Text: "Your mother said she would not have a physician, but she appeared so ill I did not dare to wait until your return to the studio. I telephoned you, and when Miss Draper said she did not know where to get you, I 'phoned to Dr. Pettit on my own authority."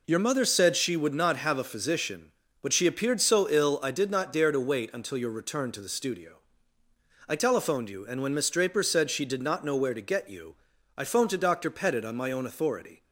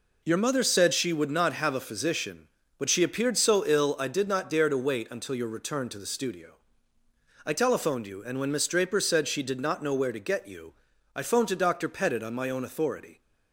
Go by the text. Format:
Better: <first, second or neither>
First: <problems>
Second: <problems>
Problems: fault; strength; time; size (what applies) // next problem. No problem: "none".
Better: neither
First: none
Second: none